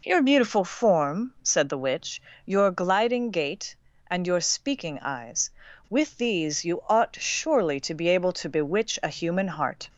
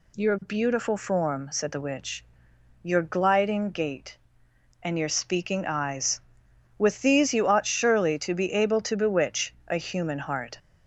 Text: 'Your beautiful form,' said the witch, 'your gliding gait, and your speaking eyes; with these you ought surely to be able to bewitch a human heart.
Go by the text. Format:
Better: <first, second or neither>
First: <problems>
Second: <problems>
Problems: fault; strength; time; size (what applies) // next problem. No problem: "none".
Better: neither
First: none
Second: none